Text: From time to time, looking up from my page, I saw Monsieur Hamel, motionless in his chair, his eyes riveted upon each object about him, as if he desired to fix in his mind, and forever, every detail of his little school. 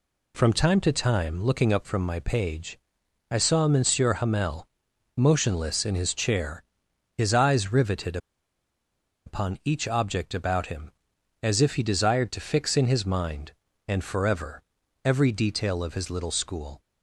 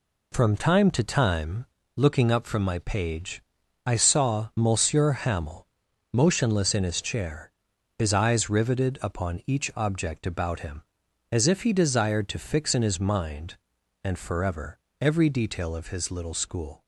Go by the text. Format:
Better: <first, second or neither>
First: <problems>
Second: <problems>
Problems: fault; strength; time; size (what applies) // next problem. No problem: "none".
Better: second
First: pauses between "riveted" and "upon"; at 8.1 s; 1.0 s long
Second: none